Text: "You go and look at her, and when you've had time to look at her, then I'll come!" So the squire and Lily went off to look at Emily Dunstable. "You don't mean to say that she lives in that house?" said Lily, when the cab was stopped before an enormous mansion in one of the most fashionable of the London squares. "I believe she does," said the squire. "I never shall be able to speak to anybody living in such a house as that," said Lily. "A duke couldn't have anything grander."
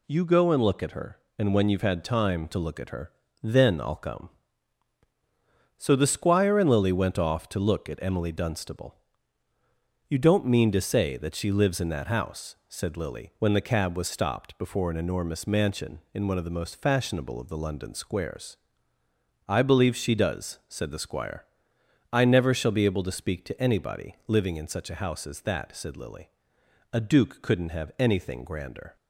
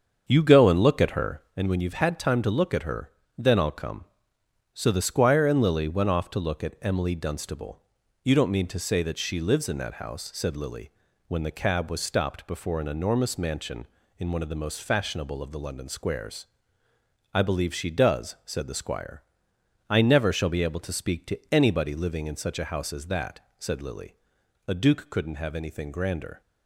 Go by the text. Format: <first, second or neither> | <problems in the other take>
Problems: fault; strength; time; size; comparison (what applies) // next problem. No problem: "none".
first | starts louder than the rest; until 1.6 s; 7 dB // pauses between "to" and "anybody"; slight; at 21.3 s; 0.16 s long